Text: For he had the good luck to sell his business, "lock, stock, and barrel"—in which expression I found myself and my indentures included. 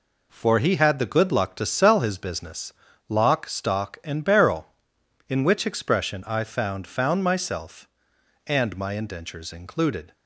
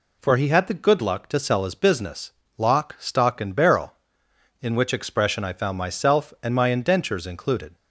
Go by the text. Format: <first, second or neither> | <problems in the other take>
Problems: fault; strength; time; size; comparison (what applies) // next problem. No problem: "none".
second | says "found" twice; at 6.8 s